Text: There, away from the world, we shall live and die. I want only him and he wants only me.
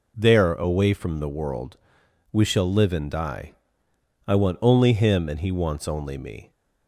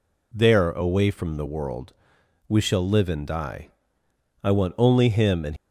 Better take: first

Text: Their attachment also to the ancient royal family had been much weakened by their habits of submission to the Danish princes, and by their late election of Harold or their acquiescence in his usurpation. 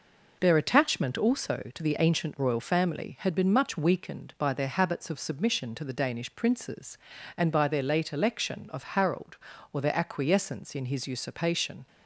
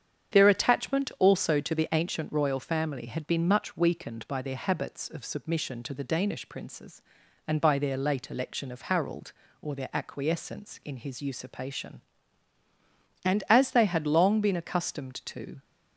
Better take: first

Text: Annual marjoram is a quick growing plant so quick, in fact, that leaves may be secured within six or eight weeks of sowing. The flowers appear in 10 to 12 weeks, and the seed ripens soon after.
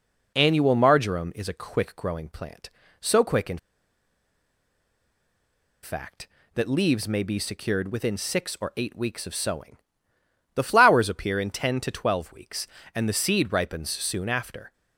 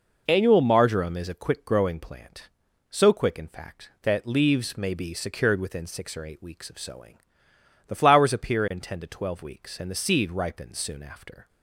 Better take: second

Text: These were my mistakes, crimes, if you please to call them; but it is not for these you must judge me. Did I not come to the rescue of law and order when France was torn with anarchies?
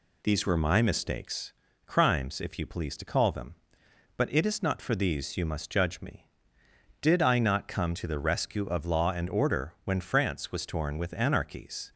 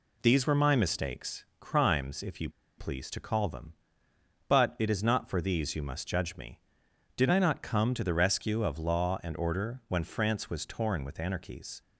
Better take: first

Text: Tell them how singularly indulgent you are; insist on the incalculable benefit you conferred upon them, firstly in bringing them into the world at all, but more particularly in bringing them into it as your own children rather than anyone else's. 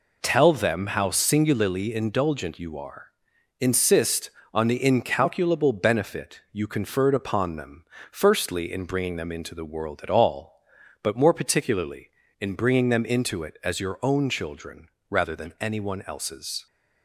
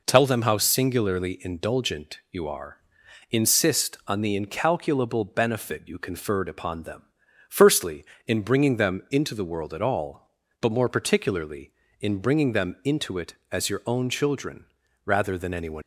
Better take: first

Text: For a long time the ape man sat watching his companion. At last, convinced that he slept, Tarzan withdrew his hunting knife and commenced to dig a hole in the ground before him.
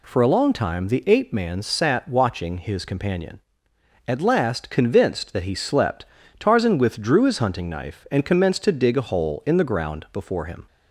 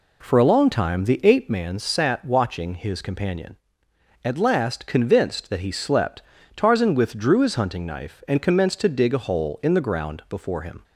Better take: first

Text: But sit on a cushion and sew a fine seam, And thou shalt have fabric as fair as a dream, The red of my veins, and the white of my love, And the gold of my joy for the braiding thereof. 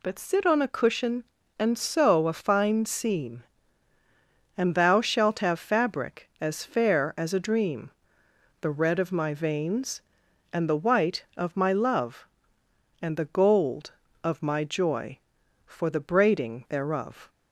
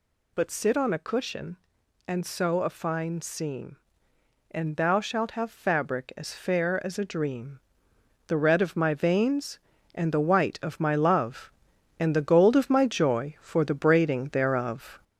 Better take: first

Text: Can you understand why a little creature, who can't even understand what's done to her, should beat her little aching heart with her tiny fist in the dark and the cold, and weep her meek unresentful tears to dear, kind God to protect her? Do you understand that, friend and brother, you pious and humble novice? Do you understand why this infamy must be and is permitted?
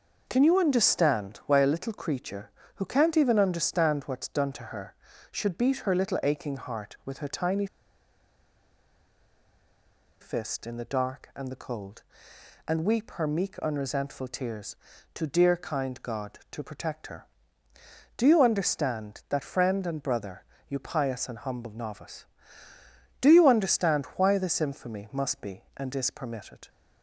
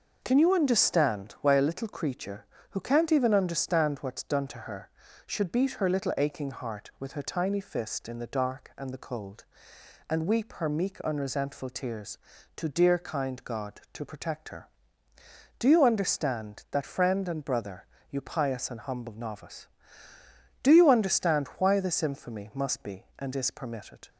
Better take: second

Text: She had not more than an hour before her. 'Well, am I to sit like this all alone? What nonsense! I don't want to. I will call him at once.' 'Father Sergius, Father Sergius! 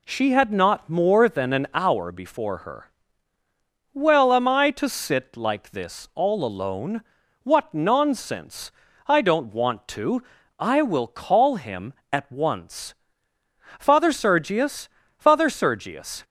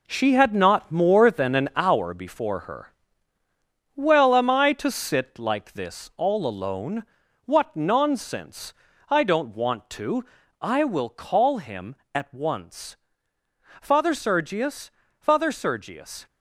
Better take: first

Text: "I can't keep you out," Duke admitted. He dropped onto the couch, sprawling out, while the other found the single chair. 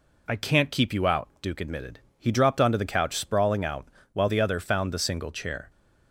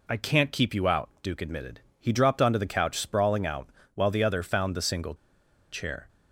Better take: first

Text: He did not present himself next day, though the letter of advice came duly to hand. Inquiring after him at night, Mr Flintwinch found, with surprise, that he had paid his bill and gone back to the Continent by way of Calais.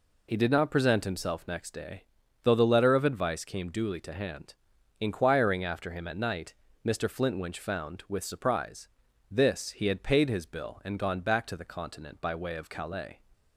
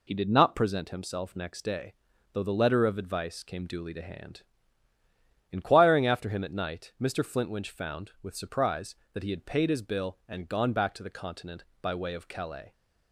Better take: second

